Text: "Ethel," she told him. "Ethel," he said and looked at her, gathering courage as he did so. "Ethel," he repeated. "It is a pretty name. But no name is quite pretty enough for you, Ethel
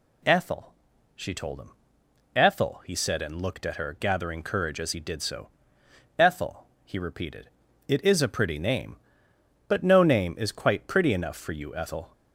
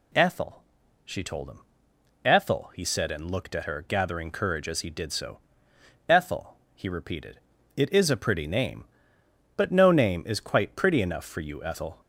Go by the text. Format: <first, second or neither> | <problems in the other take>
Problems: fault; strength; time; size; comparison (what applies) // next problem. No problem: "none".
neither | none